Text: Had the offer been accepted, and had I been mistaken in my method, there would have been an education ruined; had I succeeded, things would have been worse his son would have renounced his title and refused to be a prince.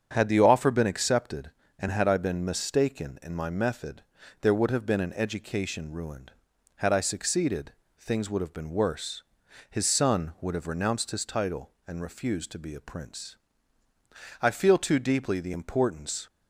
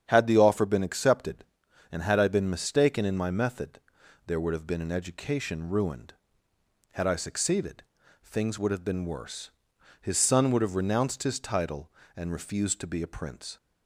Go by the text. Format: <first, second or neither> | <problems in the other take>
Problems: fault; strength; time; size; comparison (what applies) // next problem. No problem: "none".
second | starts louder than the rest; strong; until 1.1 s; 7.5 dB; strong in the second // pauses between "worse" and "his"; noticeable; at 9.2 s; 0.46 s long; noticeable in the second // goes on to say "I feel too deeply the importance"; strong; from 14.4 s on; 1.8 s long